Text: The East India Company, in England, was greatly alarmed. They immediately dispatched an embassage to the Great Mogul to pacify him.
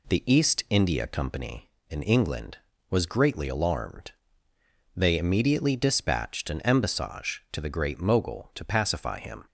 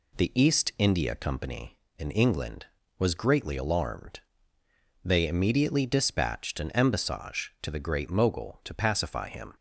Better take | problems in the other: neither | none

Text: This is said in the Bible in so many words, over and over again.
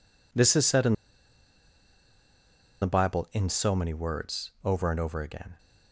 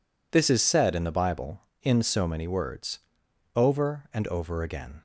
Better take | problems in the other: second | pauses between "in" and "the"; strong; at 0.9 s; 1.8 s long

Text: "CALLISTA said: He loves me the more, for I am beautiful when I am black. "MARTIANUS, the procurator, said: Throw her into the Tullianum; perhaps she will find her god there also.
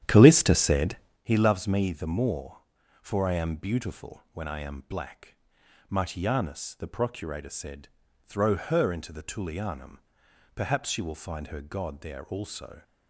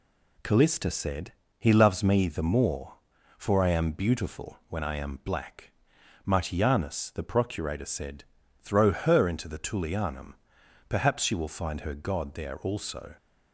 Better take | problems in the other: second | starts louder than the rest; strong; until 1.3 s; 10.5 dB

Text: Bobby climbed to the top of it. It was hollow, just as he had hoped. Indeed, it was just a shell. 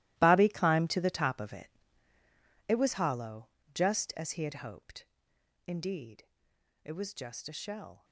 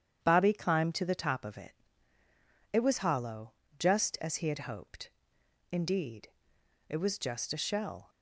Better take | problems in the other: second | gets quieter; strong; throughout; 14 dB // starts louder than the rest; strong; until 1.1 s; 16.5 dB; strong in the second

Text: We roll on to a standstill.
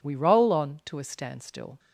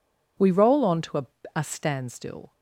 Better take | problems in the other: first | says "a" twice; at 1.5 s

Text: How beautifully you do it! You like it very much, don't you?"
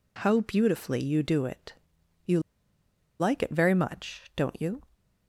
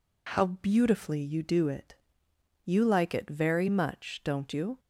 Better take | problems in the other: second | pauses between "You" and "like"; noticeable; at 2.3 s; 0.80 s long

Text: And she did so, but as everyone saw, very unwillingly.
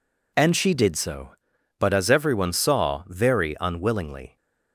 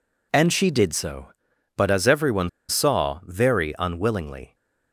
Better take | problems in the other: first | pauses between "everyone" and "saw"; slight; at 2.4 s; 0.20 s long

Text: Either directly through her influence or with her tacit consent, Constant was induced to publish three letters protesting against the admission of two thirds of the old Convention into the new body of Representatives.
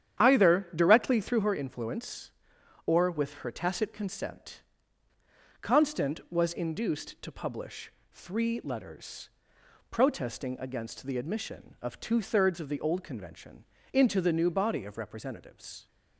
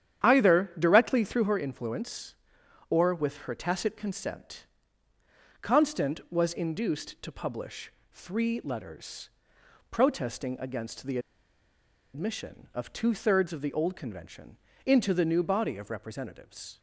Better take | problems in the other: first | starts louder than the rest; strong; until 1.3 s; 9.5 dB; strong in the first // pauses between "publish" and "three"; slight; at 7.9 s; 0.22 s long; slight in the first // pauses between "letters" and "protesting"; noticeable; at 9.2 s; 0.62 s long; noticeable in the first // pauses between "the" and "admission"; noticeable; at 11.1 s; 0.95 s long // pauses between "Convention" and "into"; slight; at 14.5 s; 0.28 s long; slight in the first

